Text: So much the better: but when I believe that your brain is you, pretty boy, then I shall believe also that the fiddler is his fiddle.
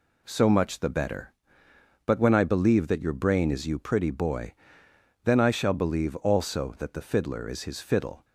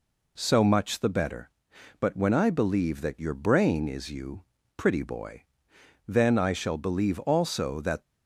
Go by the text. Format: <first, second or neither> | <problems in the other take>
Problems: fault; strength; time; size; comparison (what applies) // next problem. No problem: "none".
first | stops before "the fiddler is his fiddle"; at 8.0 s